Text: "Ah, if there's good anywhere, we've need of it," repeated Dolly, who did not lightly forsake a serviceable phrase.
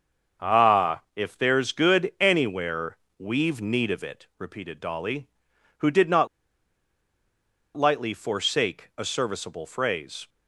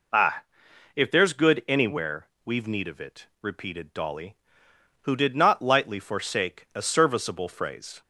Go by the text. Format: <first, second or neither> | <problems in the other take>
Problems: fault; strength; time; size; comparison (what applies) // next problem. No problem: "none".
second | starts louder than the rest; until 1.5 s; 7 dB // pauses between "not" and "lightly"; strong; at 6.2 s; 1.4 s long